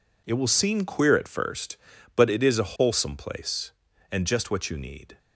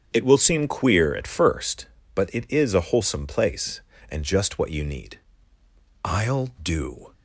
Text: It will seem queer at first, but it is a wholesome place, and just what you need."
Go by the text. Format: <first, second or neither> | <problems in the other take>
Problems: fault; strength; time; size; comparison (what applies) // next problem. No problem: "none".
first | starts louder than the rest; strong; until 1.1 s; 8 dB // goes on to say "I'll do"; noticeable; from 6.0 s on; 1.1 s long